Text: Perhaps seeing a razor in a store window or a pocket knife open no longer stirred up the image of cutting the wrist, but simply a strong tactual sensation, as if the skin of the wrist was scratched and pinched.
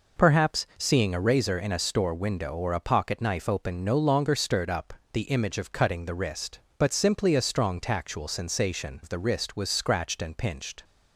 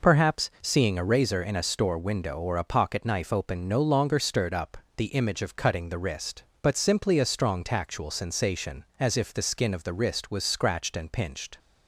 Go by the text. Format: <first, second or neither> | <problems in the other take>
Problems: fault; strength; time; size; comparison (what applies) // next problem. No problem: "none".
second | pauses between "up" and "the"; slight; at 4.9 s; 0.20 s long; slight in the second // skips "as if the skin"; at 9.0 s